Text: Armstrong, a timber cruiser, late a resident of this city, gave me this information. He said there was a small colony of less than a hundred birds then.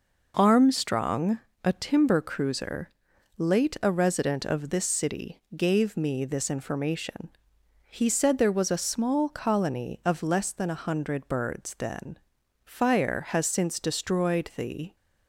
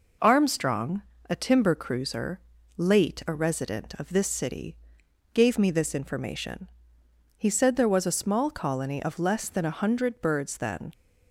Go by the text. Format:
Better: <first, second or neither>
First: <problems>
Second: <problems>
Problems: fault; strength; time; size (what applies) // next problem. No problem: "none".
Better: second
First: goes on to say "Fire has since destroyed the"; strong; from 12.6 s on; 2.3 s long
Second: none